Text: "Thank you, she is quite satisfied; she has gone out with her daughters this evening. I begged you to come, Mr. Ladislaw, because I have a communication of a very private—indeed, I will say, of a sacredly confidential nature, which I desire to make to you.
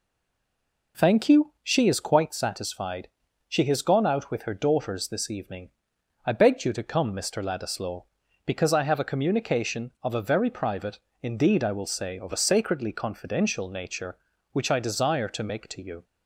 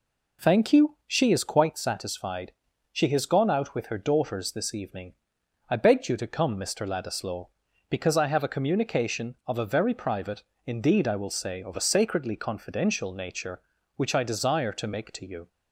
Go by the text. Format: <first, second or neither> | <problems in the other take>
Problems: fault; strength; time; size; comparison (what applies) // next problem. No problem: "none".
second | stays silent before the first word; slight; until 0.9 s; 0.9 s long